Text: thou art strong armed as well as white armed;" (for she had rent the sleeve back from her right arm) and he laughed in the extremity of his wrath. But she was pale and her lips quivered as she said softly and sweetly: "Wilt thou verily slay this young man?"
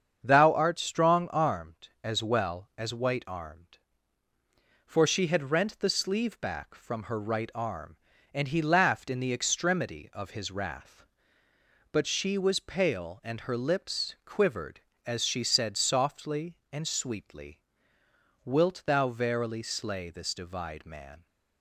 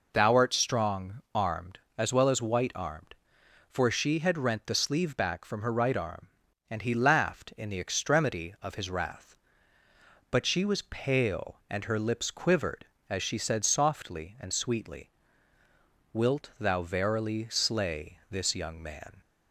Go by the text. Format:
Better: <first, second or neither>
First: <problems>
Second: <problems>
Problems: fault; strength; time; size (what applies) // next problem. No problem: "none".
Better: second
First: starts louder than the rest; strong; until 1.2 s; 7.5 dB // says "divide" for "young"; at 20.3 s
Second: none